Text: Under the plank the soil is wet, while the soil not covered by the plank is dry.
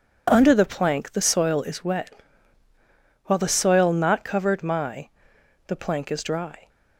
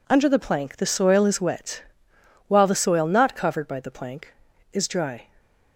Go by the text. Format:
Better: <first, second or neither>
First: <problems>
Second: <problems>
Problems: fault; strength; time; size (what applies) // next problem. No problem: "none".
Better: second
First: says "my" for "by"; at 4.6 s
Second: none